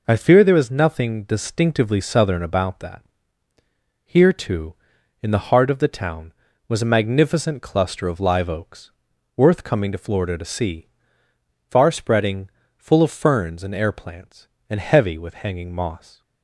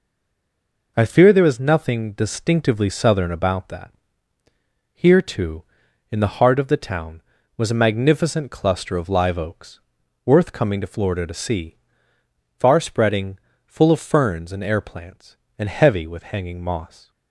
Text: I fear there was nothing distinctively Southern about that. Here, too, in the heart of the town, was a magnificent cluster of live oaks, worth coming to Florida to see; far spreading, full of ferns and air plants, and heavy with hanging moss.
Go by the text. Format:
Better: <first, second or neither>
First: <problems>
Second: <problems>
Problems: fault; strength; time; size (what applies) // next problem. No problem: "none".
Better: first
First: none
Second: stays silent before the first word; slight; until 0.9 s; 0.9 s long